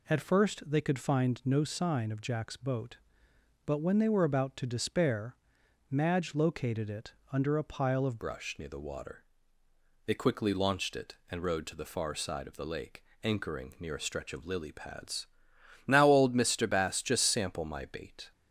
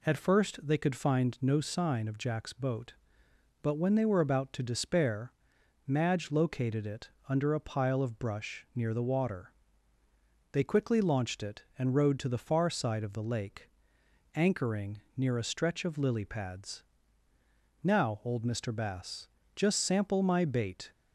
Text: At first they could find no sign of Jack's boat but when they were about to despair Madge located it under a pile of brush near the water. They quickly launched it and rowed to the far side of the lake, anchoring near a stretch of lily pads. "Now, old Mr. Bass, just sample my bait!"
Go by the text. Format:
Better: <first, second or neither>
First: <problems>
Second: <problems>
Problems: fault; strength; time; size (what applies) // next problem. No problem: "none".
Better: second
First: pauses between "despair" and "Madge"; noticeable; at 5.3 s; 0.54 s long // pauses between "it" and "under"; slight; at 7.1 s; 0.20 s long // changes voice at "brush"; from 8.1 s on; 10.2 s long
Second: pauses between "despair" and "Madge"; noticeable; at 5.3 s; 0.54 s long // pauses between "it" and "under"; slight; at 7.0 s; 0.20 s long